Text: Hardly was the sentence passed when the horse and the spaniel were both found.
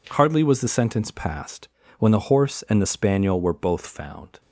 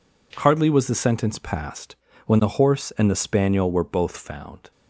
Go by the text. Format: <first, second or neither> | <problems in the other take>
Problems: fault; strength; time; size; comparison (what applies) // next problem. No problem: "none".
neither | pauses between "passed" and "when"; slight; the same in both